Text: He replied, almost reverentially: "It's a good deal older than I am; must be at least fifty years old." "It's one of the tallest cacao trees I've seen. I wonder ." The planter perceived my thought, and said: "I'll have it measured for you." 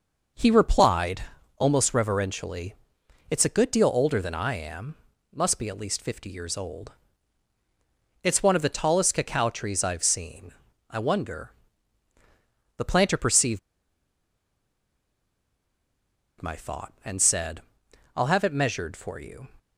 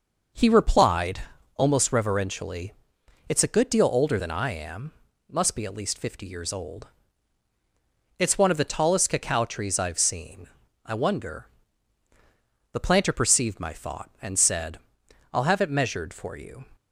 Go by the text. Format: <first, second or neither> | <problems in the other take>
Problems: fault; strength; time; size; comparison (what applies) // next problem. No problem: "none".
second | pauses between "perceived" and "my"; strong; at 13.5 s; 2.8 s long